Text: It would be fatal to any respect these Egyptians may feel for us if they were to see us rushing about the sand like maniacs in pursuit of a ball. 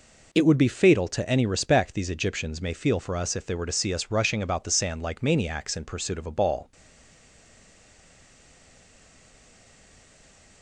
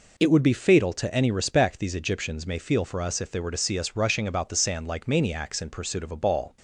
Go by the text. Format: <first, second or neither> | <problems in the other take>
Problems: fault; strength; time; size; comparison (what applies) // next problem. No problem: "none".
second | stays silent after the last word; strong; from 6.7 s on; 3.9 s long